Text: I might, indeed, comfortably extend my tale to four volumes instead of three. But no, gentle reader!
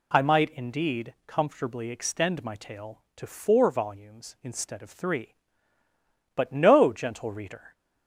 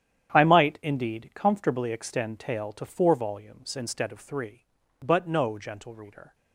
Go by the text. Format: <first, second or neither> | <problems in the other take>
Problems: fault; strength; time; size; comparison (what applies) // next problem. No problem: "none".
first | starts louder than the rest; strong; until 1.3 s; 9.5 dB // skips "my"; at 2.3 s